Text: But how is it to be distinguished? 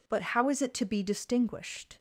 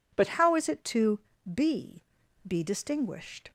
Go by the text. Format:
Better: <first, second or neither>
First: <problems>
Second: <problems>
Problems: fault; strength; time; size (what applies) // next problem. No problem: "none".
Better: first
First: none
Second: pauses between "to" and "be"; slight; at 1.1 s; 0.36 s long // says "be" twice; at 2.4 s